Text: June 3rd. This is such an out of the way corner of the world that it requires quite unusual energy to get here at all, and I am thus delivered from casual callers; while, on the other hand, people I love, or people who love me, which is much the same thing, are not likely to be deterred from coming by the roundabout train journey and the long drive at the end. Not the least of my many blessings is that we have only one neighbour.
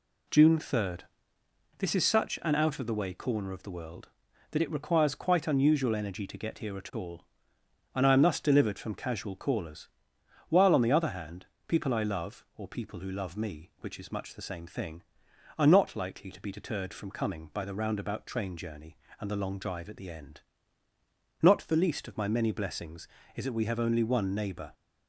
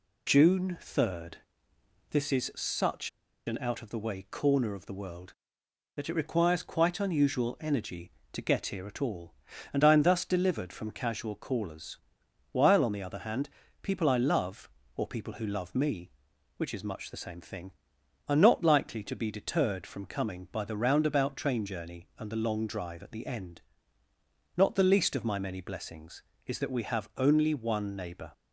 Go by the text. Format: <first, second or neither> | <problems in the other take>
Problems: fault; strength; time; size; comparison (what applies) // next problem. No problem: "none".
first | pauses between "such" and "an"; at 3.0 s; 0.37 s long